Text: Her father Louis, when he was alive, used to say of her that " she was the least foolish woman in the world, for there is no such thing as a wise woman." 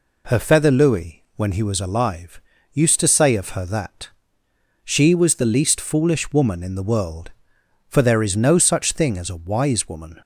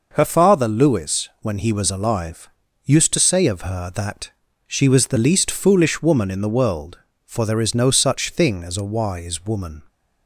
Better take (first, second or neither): second